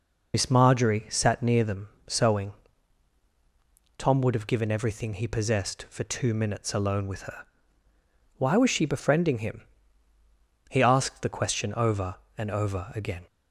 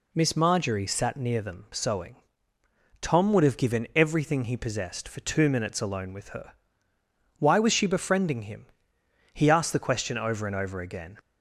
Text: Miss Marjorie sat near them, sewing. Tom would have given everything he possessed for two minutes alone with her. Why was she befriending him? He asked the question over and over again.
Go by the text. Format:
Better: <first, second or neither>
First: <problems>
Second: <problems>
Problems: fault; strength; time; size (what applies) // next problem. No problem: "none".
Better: second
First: loses the start of "Miss"; at 0.3 s; 70 ms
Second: none